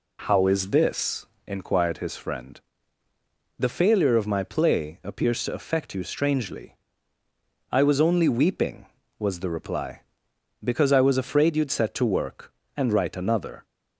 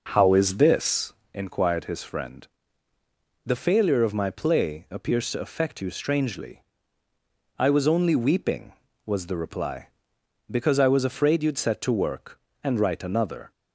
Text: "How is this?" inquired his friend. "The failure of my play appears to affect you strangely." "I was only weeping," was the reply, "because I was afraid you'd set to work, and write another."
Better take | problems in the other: first | starts louder than the rest; noticeable; until 1.2 s; 5.5 dB

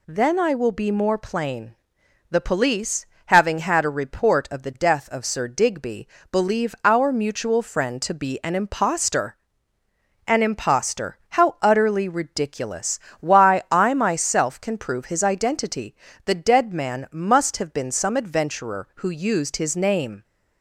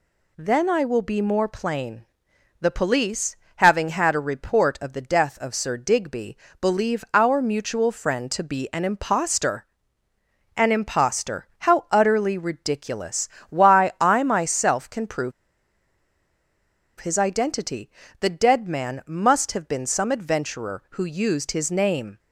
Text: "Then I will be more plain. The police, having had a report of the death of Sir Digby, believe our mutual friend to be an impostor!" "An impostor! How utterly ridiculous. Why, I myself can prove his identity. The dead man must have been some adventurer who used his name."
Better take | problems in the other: first | pauses between "prove" and "his"; strong; at 15.3 s; 1.6 s long

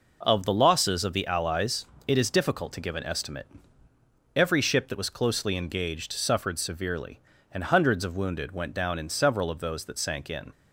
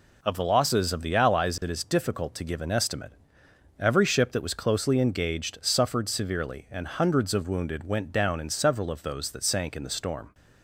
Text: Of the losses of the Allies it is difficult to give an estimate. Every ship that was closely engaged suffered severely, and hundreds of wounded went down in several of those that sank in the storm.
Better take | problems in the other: second | pauses between "Allies" and "it"; slight; at 1.8 s; 0.20 s long // stops before "the storm"; at 10.5 s

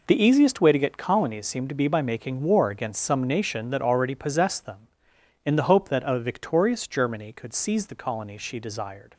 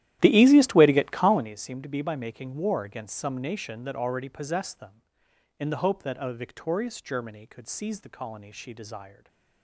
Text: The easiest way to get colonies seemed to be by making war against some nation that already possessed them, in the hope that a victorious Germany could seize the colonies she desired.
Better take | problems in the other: first | starts louder than the rest; strong; until 1.5 s; 13 dB // stays silent after the last word; slight; from 9.1 s on; 0.5 s long

